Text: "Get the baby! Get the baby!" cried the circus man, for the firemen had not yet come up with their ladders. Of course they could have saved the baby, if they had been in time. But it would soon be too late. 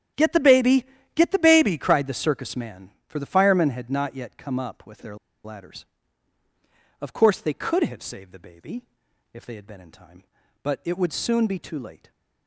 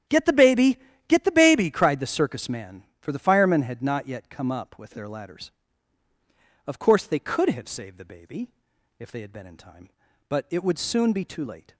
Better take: second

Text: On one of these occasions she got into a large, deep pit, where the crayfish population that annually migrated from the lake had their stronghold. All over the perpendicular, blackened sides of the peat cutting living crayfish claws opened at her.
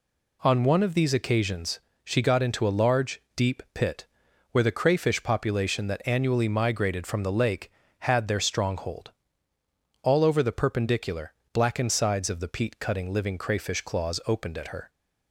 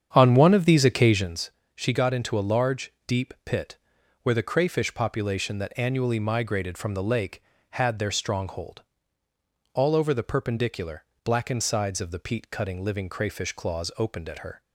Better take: first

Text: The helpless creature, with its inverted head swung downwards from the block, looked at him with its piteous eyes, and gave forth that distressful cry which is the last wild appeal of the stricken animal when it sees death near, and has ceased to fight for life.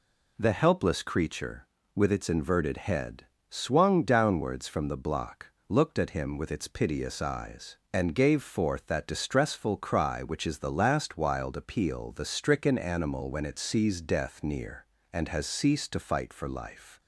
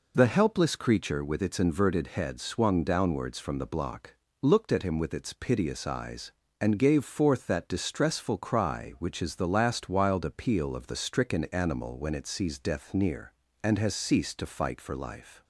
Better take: second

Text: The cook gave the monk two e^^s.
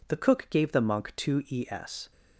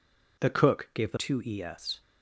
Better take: first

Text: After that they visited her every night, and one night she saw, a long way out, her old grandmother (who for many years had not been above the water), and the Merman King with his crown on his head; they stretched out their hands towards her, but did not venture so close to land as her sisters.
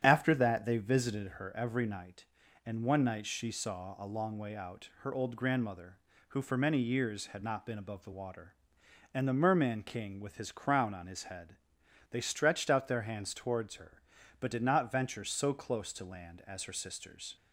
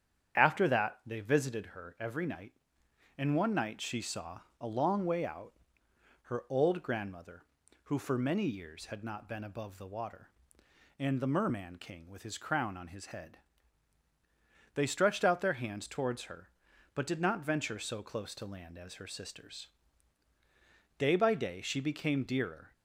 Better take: first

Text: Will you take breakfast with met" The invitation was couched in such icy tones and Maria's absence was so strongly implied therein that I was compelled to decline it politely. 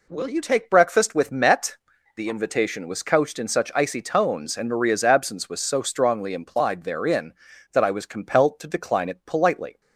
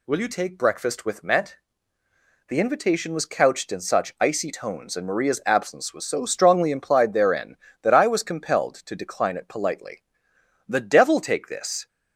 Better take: first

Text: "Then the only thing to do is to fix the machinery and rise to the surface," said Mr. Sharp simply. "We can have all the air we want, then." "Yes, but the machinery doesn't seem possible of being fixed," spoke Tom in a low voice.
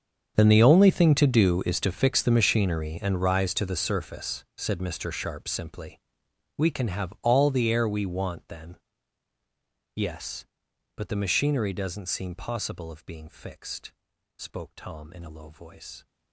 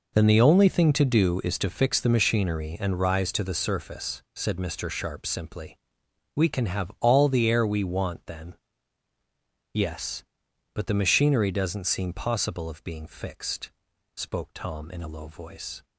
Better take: second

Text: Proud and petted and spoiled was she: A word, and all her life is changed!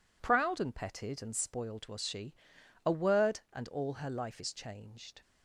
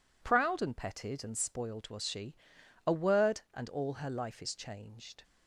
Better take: neither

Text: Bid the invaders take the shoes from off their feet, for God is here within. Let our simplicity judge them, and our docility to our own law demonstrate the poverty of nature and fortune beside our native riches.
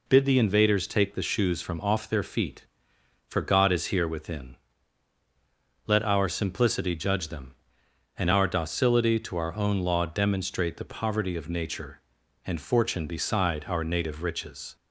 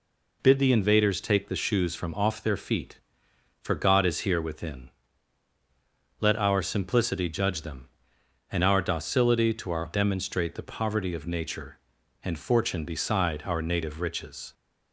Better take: first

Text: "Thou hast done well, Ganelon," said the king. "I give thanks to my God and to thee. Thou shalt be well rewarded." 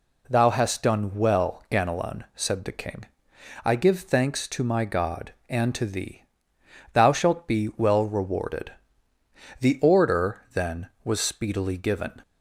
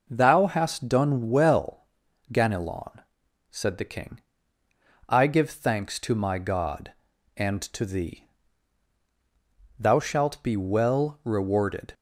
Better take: second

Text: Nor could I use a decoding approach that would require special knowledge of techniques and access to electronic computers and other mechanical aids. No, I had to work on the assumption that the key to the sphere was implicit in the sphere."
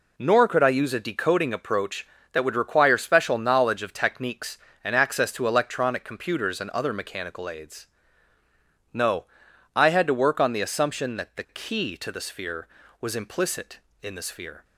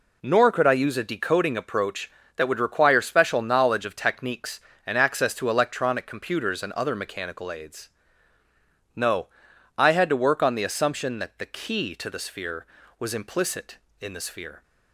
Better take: neither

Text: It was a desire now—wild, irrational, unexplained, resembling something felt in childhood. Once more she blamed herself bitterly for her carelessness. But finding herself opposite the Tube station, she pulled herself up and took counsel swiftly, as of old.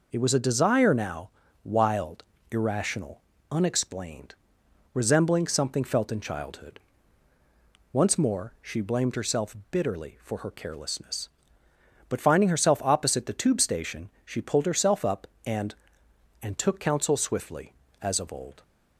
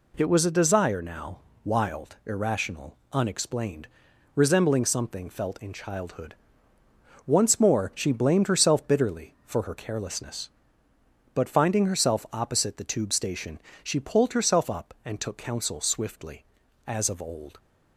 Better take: second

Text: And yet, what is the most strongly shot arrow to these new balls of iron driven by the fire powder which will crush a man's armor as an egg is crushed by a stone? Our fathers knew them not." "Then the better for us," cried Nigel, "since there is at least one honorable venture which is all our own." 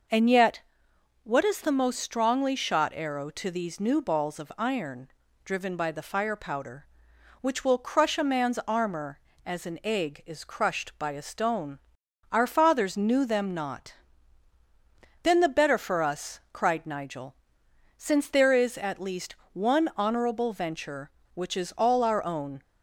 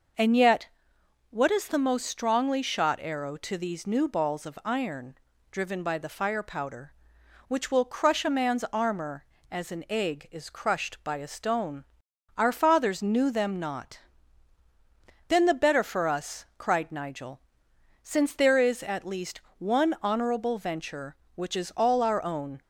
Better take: neither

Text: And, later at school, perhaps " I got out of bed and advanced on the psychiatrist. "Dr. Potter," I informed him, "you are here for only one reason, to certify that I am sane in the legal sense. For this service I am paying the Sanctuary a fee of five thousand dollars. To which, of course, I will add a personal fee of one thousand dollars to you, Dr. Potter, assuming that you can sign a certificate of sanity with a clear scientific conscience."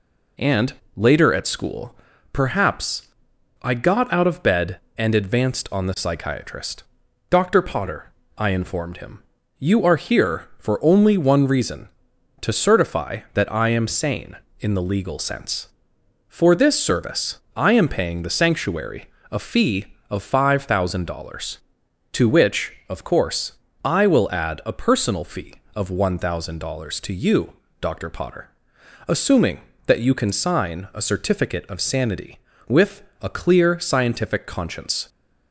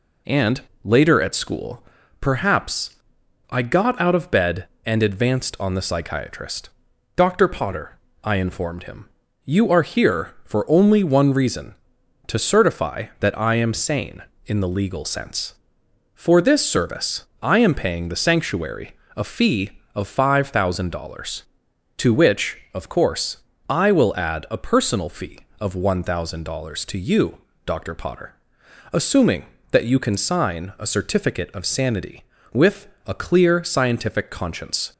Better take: neither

